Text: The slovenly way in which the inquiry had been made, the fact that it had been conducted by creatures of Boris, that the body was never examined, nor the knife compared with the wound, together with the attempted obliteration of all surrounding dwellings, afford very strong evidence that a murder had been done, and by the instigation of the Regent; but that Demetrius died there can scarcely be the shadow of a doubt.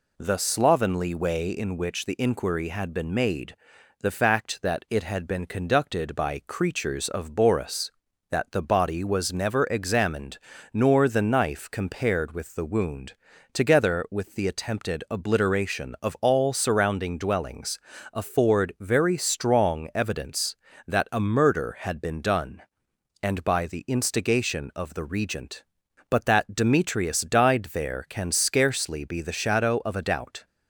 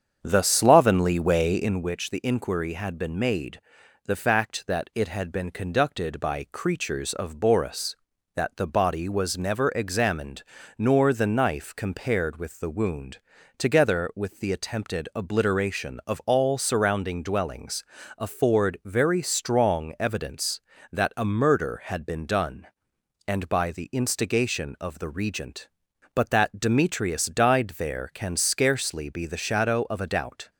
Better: first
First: none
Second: starts louder than the rest; strong; until 1.9 s; 7.5 dB

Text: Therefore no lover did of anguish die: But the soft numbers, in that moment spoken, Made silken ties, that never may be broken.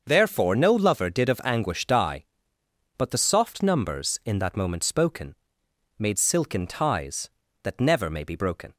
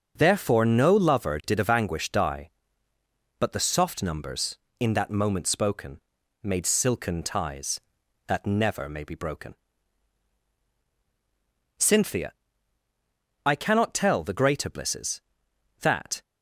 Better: first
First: starts louder than the rest; until 1.0 s; 6.5 dB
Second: starts louder than the rest; until 1.1 s; 6.5 dB // goes on to say "Cynthia I cannot tell the greater blisses That"; strong; from 11.7 s on; 4.4 s long

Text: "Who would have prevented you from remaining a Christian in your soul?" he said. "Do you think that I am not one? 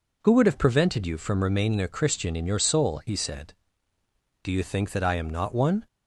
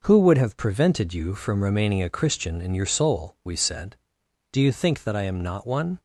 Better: first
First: none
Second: says "we" for "he"; at 3.4 s

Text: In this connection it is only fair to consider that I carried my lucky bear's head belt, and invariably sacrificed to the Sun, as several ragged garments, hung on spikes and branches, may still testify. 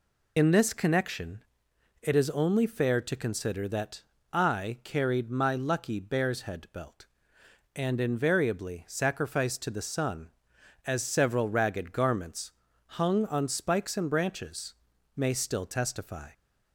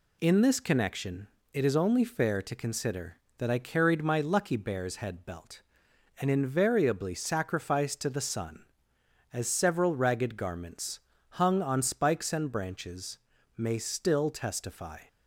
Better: second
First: loses the start of "In"; at 0.3 s; 70 ms // pauses between "connection" and "it"; noticeable; at 1.4 s; 0.60 s long // pauses between "that" and "I"; slight; at 4.0 s; 0.28 s long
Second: pauses between "connection" and "it"; slight; at 1.2 s; 0.24 s long

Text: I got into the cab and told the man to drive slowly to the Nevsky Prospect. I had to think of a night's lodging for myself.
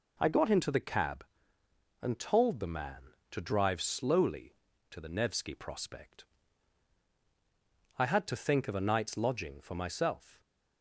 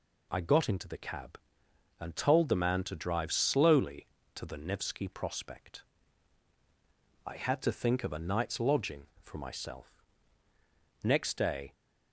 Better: first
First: none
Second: goes on to say "Next day"; noticeable; from 11.0 s on; 0.70 s long

